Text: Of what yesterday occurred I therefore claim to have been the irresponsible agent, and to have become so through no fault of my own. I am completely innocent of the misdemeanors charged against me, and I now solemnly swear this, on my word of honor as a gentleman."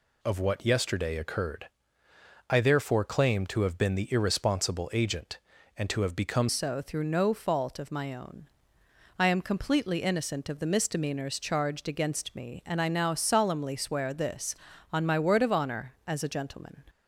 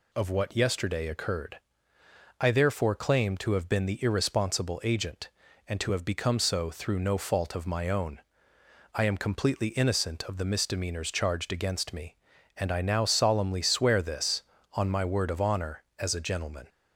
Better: second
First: pauses between "occurred" and "I"; noticeable; at 1.6 s; 0.80 s long // changes voice at "so"; from 6.4 s on; 10.4 s long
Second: pauses between "occurred" and "I"; noticeable; at 1.5 s; 0.80 s long

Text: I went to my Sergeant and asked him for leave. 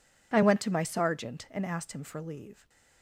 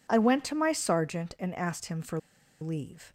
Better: first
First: none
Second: pauses between "for" and "leave"; at 2.1 s; 0.43 s long

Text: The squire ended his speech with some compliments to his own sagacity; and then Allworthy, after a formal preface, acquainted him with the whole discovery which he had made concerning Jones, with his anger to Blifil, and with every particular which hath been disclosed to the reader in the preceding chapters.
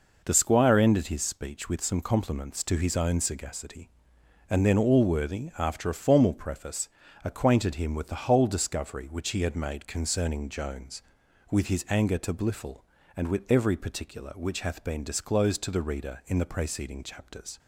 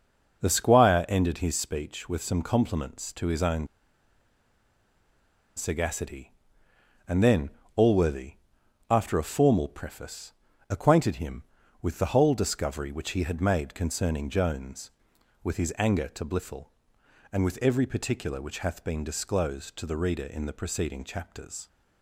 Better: first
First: none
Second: pauses between "own" and "sagacity"; strong; at 3.6 s; 1.9 s long // pauses between "then" and "Allworthy"; slight; at 7.5 s; 0.24 s long

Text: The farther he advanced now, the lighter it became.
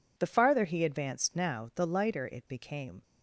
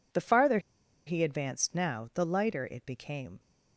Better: first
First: none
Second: pauses between "farther" and "he"; noticeable; at 0.5 s; 0.47 s long

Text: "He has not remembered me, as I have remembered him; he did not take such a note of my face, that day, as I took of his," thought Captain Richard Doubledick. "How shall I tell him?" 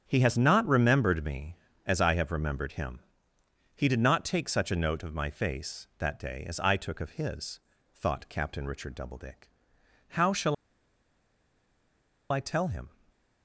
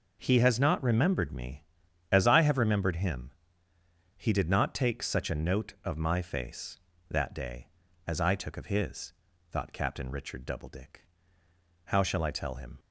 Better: second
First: starts louder than the rest; strong; until 1.0 s; 8 dB // pauses between "shall" and "I"; strong; at 10.5 s; 1.7 s long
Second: none

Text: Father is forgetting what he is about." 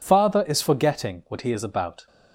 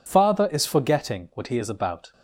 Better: neither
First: none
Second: none

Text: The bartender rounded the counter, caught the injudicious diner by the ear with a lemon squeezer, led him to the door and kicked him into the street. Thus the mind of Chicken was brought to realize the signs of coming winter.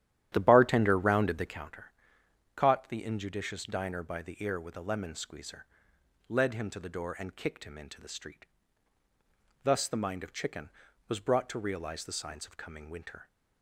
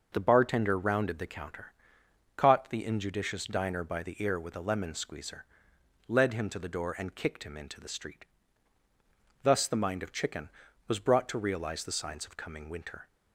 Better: second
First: starts louder than the rest; strong; until 1.7 s; 11.5 dB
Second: none

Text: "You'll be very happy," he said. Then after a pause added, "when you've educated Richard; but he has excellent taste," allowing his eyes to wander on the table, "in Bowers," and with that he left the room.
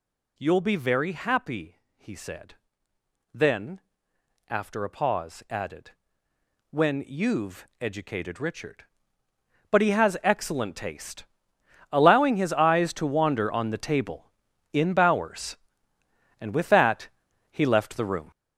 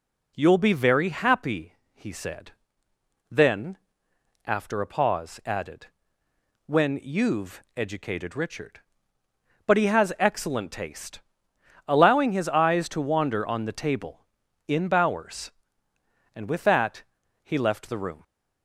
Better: second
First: gets louder; strong; throughout; 7.5 dB // pauses between "Then" and "after"; noticeable; at 3.8 s; 0.68 s long // pauses between "that" and "he"; at 17.0 s; 0.42 s long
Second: pauses between "Then" and "after"; noticeable; at 3.7 s; 0.68 s long // pauses between "that" and "he"; at 17.0 s; 0.40 s long

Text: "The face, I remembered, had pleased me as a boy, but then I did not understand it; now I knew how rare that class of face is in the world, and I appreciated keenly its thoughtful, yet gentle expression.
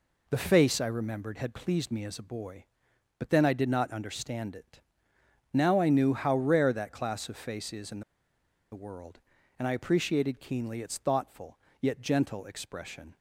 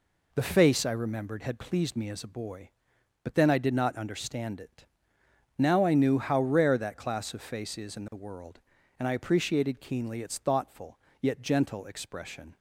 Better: second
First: pauses between "in" and "the"; noticeable; at 8.0 s; 0.71 s long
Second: none

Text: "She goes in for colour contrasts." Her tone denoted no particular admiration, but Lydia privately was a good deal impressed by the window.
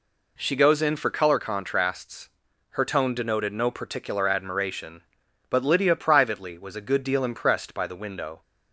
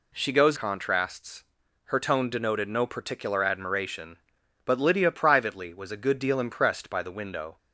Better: first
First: none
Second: skips "in for colour"; at 0.5 s

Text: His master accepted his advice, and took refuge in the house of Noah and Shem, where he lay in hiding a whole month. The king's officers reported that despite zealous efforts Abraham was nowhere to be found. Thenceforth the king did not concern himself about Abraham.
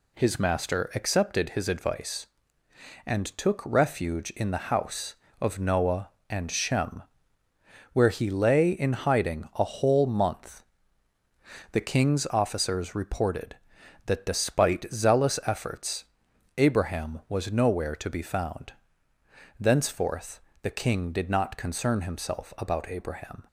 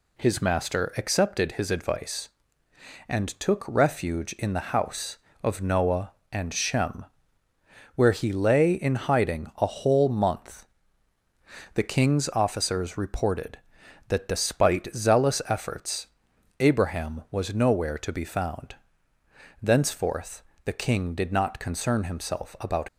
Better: first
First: pauses between "efforts" and "Abraham"; noticeable; at 16.0 s; 0.52 s long // pauses between "Thenceforth" and "the"; slight; at 20.3 s; 0.24 s long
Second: pauses between "efforts" and "Abraham"; noticeable; at 16.0 s; 0.52 s long // pauses between "Thenceforth" and "the"; slight; at 20.4 s; 0.24 s long // stops before "Abraham"; at 22.8 s

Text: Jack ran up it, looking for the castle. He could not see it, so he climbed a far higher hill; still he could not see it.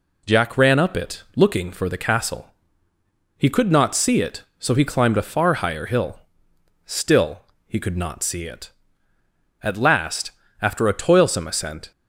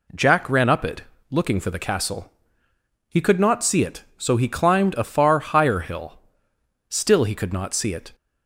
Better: second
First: pauses between "still" and "he"; slight; at 7.4 s; 0.26 s long // goes on to say "At last after a toilsome ascent"; strong; from 9.6 s on; 2.2 s long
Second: none

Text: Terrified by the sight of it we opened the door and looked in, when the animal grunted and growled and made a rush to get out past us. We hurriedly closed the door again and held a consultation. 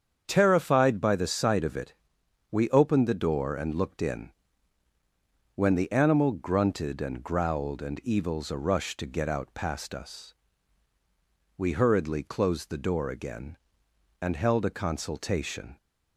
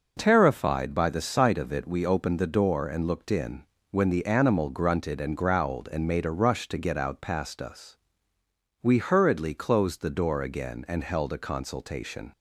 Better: second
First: starts louder than the rest; strong; until 1.2 s; 7.5 dB // pauses between "it" and "we"; noticeable; at 1.9 s; 0.56 s long // says "evils" for "made"; at 8.0 s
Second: none

